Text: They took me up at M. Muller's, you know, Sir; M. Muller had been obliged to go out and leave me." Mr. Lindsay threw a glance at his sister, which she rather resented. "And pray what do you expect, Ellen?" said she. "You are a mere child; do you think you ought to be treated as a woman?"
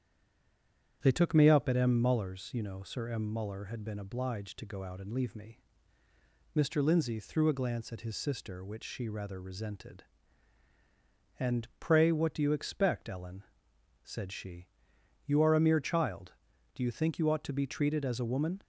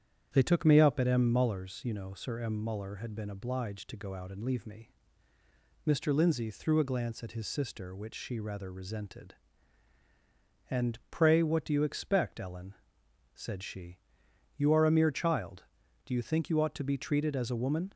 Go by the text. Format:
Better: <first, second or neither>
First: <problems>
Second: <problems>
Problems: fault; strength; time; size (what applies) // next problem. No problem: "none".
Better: second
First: stays silent before the first word; until 1.0 s; 1.0 s long // starts louder than the rest; strong; until 2.0 s; 9 dB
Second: starts louder than the rest; strong; until 1.3 s; 9 dB